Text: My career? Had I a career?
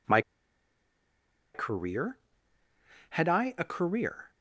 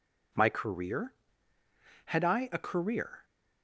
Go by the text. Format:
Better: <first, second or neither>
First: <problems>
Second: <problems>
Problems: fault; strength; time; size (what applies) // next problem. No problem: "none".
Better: second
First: pauses between "My" and "career"; strong; at 0.2 s; 1.3 s long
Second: none